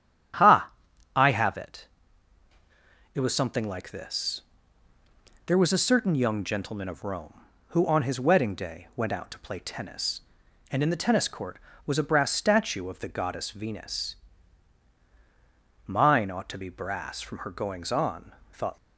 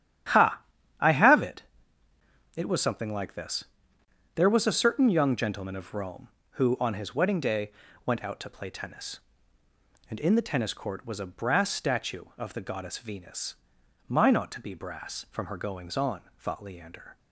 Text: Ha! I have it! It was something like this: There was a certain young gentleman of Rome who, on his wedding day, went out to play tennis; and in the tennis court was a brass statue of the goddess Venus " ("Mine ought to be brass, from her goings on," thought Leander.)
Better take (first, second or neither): second